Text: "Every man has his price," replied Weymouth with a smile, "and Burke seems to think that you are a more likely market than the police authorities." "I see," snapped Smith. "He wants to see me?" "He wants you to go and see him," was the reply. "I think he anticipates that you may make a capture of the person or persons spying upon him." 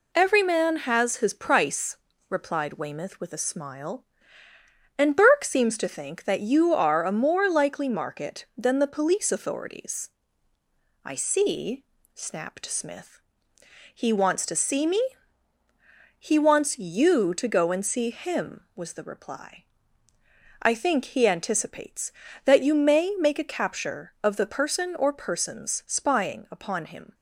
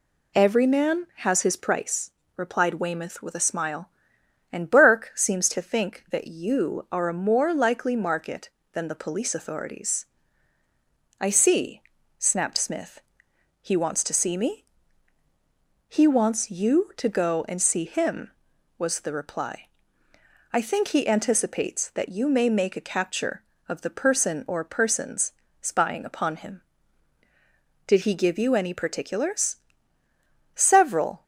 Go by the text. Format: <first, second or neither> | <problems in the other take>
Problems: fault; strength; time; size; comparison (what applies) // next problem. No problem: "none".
first | pauses between "persons" and "spying"; slight; at 25.3 s; 0.30 s long // goes on to say "Did he give you any particulars Several"; strong; from 27.8 s on; 3.3 s long